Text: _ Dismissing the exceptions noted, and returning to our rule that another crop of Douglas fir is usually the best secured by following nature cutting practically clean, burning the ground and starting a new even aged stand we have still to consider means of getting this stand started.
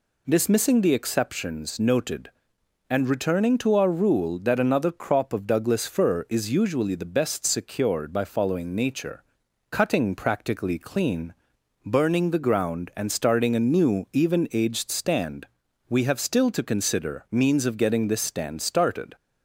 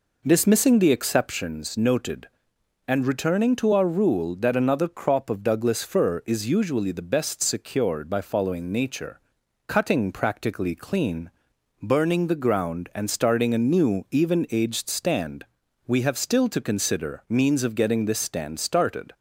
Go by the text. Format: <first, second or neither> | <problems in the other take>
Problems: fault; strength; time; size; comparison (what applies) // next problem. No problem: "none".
first | starts louder than the rest; noticeable; until 1.5 s; 4.5 dB // pauses between "nature" and "cutting"; noticeable; at 9.1 s; 0.48 s long; noticeable in the first // pauses between "stand" and "we"; at 15.4 s; 0.41 s long; also in the first